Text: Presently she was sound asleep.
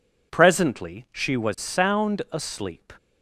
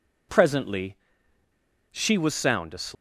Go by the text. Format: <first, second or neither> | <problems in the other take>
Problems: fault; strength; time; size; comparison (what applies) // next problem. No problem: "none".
first | pauses between "Presently" and "she"; noticeable; at 0.9 s; 0.96 s long